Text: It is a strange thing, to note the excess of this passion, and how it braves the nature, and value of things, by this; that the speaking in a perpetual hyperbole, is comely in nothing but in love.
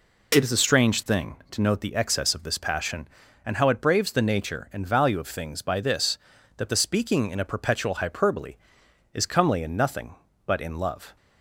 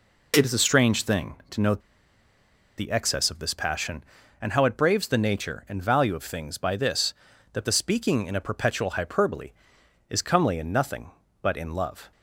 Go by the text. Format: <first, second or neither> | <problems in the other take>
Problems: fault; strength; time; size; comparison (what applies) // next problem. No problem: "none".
first | pauses between "note" and "the"; at 1.7 s; 0.98 s long